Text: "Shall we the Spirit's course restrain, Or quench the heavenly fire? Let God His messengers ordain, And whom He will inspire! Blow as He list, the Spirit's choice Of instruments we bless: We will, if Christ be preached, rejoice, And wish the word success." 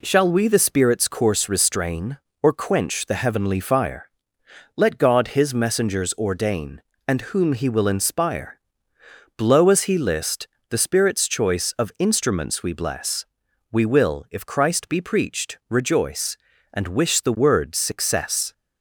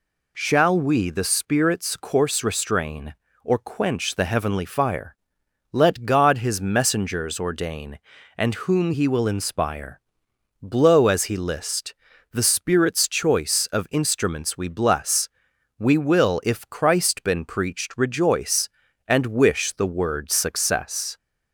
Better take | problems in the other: first | says "been" for "be"; at 17.2 s

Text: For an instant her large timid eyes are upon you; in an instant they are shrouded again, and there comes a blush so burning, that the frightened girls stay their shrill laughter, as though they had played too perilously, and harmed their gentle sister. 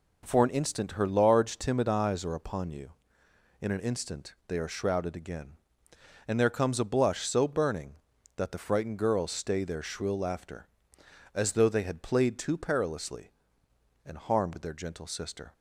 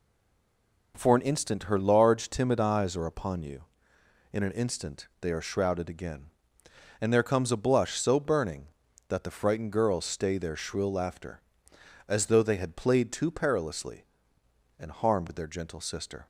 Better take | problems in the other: first | stays silent before the first word; slight; until 0.9 s; 0.9 s long

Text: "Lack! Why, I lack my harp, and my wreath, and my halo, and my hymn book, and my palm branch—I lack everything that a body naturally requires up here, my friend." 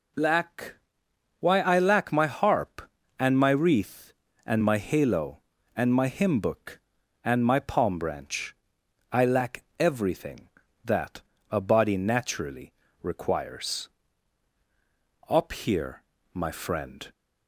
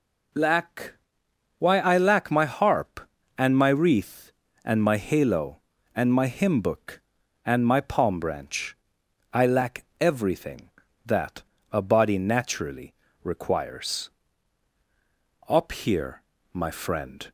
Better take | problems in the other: neither | pauses between "that" and "a"; slight; the same in both // pauses between "naturally" and "requires"; slight; the same in both // pauses between "requires" and "up"; strong; the same in both

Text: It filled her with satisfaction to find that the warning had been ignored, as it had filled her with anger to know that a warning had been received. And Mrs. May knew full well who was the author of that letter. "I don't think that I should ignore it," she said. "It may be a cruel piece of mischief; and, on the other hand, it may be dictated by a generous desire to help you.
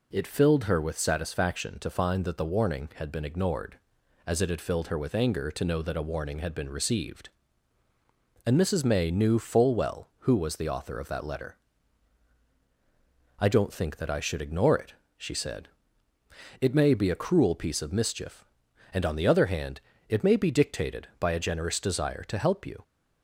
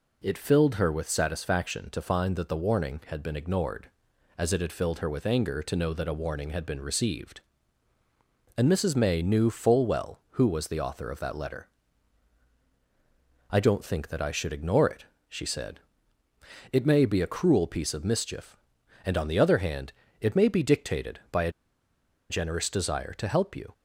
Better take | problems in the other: first | pauses between "a" and "generous"; noticeable; at 21.5 s; 0.79 s long

